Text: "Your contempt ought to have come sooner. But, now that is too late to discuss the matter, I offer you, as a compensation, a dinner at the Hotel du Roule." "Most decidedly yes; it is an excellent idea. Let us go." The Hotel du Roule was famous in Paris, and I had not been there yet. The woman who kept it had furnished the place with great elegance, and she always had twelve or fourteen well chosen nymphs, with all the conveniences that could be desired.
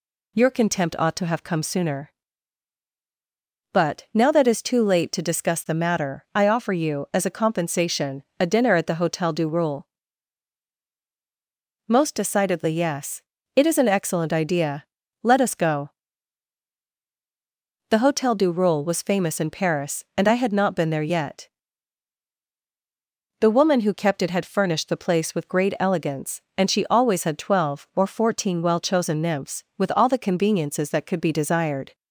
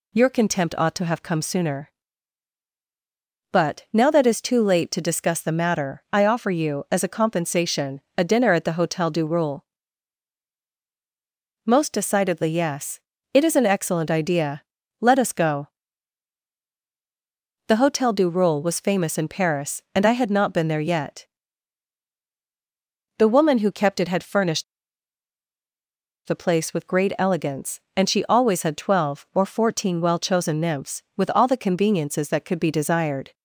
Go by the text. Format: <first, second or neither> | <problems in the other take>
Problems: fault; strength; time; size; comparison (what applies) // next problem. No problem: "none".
first | pauses between "furnished" and "the"; strong; at 24.6 s; 1.6 s long